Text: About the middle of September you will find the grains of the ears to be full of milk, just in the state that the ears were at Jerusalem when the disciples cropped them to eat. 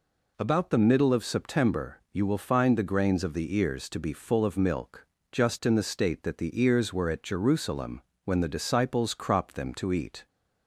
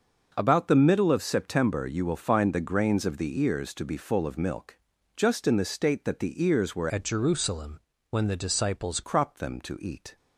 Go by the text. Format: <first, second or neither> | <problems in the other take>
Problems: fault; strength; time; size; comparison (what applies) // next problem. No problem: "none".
first | starts louder than the rest; until 1.3 s; 6.5 dB // changes voice from "at" to "disciples"; from 6.8 to 9.0 s; 2.2 s long // pauses between "Jerusalem" and "when"; slight; at 7.7 s; 0.30 s long; slight in the first